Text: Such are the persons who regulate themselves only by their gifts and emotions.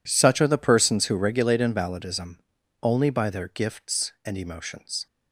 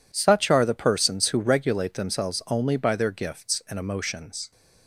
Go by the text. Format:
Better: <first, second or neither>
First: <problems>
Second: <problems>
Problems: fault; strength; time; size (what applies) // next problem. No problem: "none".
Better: second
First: says "invalidism" for "themselves"; at 1.6 s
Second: none